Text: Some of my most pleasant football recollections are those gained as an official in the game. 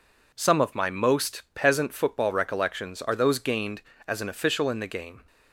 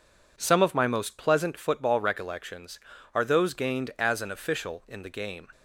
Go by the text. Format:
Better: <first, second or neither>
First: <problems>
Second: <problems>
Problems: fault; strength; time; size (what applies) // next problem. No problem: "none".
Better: second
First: says "peasant" for "pleasant"; at 1.5 s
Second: none